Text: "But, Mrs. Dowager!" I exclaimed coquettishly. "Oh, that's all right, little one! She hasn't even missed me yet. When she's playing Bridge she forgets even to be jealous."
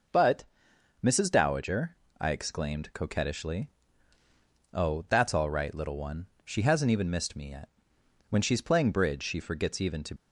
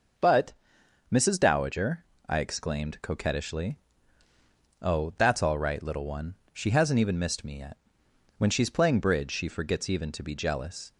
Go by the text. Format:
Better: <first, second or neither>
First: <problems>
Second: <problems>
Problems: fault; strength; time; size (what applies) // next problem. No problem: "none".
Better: second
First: stops before "be jealous"; at 10.1 s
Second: none